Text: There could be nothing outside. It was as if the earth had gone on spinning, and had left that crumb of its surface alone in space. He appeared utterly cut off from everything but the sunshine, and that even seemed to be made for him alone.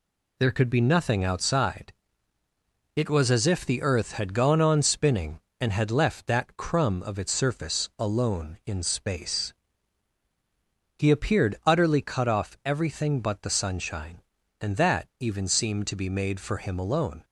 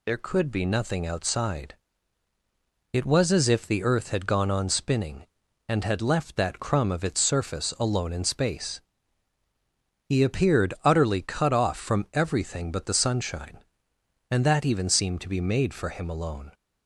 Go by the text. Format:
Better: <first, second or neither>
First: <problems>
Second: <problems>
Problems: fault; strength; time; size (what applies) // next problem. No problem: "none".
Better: second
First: skips "from"; at 12.6 s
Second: none